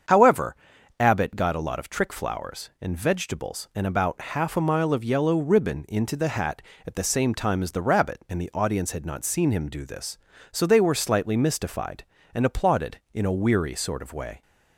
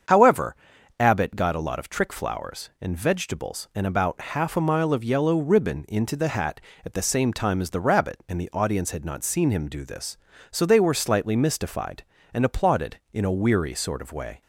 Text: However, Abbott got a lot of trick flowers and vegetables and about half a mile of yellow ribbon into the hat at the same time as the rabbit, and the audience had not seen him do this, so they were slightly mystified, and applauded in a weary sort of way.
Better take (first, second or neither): neither